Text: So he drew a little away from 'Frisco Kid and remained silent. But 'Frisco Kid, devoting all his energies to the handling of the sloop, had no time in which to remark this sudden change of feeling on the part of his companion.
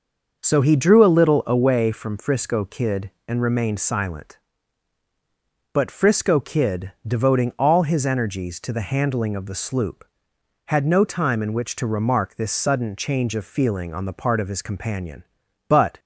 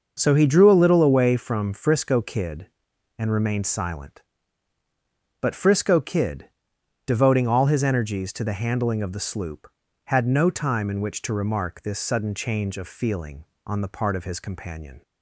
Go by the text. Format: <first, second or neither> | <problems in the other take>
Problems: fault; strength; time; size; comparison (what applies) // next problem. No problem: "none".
second | starts louder than the rest; noticeable; until 1.4 s; 6 dB; noticeable in the second // goes on to say "But"; slight; from 15.6 s on; 0.32 s long